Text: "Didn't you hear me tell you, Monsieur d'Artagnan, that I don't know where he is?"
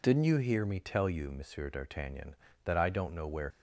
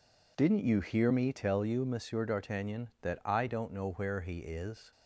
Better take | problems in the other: second | stops before "he is"; at 3.5 s

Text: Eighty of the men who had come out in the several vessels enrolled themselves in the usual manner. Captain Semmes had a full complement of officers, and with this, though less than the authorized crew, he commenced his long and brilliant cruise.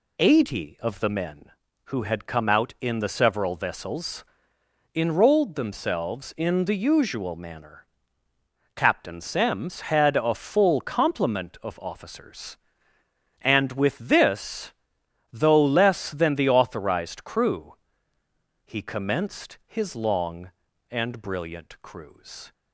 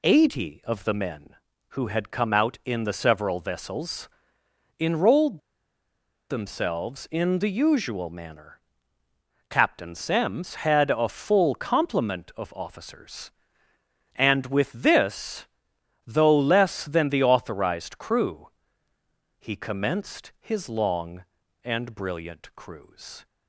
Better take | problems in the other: first | pauses between "vessels" and "enrolled"; noticeable; at 4.0 s; 0.70 s long; noticeable in the first // pauses between "enrolled" and "themselves"; noticeable; at 5.3 s; 0.89 s long

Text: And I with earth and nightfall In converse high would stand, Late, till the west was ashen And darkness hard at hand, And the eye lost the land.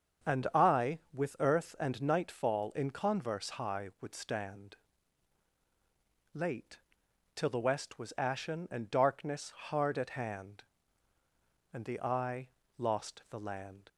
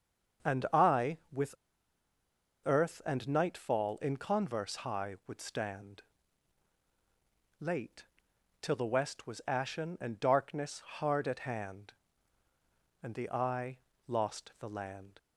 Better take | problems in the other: first | starts louder than the rest; until 2.7 s; 7 dB; also in the first // pauses between "with" and "earth"; at 1.5 s; 1.1 s long // pauses between "eye" and "lost"; slight; at 13.7 s; 0.30 s long; slight in the first

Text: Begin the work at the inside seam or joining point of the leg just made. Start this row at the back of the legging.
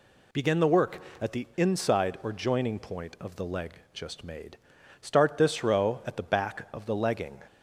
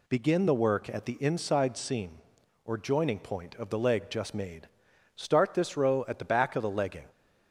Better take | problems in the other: second | skips "seam"; at 2.2 s // pauses between "leg" and "just"; slight; at 3.7 s; 0.20 s long

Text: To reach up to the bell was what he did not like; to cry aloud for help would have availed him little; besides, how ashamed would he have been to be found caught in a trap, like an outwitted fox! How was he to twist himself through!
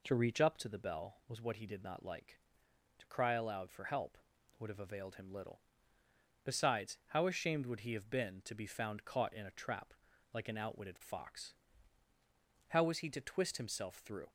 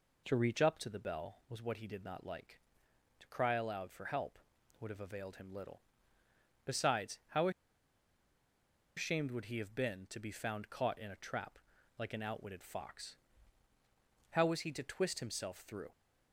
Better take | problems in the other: first | pauses between "how" and "ashamed"; strong; at 7.4 s; 1.4 s long

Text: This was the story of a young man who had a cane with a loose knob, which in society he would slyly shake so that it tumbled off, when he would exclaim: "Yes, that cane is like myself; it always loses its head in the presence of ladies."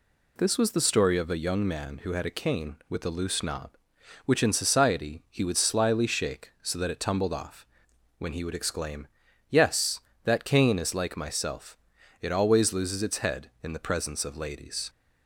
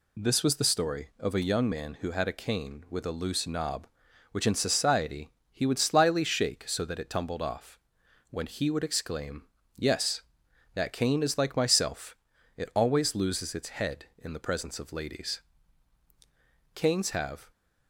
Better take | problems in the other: first | pauses between "society" and "he"; slight; at 5.2 s; 0.22 s long // goes on to say "Canes have"; noticeable; from 16.7 s on; 0.78 s long

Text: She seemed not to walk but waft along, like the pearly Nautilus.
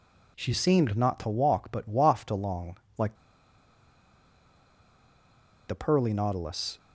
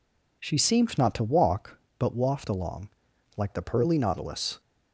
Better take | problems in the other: second | pauses between "like" and "the"; strong; at 3.1 s; 2.5 s long

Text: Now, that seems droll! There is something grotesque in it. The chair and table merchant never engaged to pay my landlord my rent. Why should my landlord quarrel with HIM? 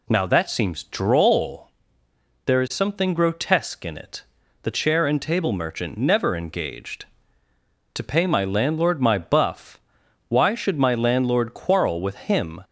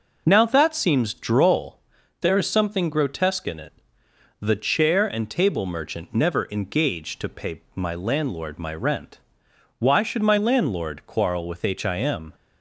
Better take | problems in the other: second | says "buff" for "rent"; at 9.1 s

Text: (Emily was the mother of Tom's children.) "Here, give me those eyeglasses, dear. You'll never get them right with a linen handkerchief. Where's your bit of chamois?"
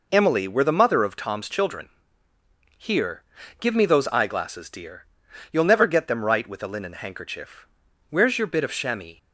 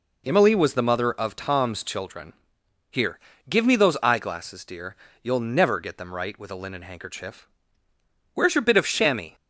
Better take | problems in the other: second | says "were" for "was"; at 0.4 s

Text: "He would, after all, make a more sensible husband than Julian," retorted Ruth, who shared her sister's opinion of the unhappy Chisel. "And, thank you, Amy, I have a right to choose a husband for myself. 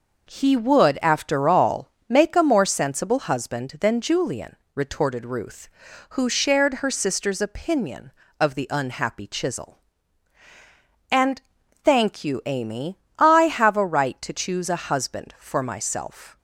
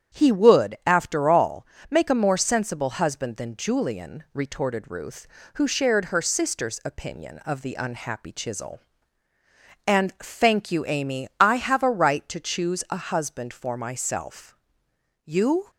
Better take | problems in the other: first | starts louder than the rest; strong; until 1.2 s; 8.5 dB // goes on to say "You"; slight; from 15.2 s on; 0.46 s long

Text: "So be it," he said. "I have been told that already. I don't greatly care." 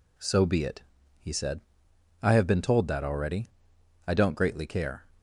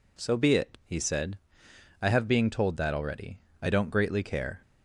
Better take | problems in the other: first | says "being" for "been"; at 2.2 s

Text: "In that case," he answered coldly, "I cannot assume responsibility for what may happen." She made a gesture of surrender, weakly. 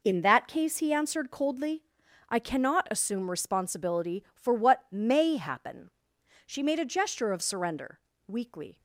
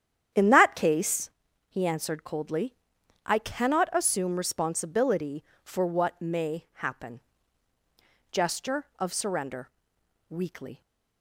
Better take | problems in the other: first | starts louder than the rest; strong; until 1.7 s; 9.5 dB // skips "She made a"; at 7.7 s

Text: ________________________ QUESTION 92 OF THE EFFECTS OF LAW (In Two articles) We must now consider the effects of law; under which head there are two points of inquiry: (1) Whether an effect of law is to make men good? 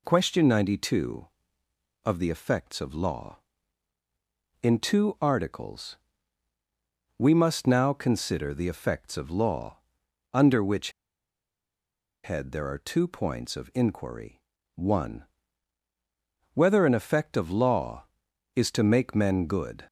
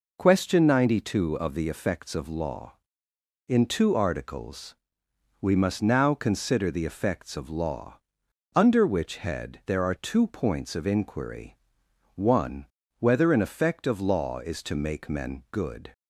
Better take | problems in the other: second | pauses between "which" and "head"; strong; at 10.9 s; 1.3 s long

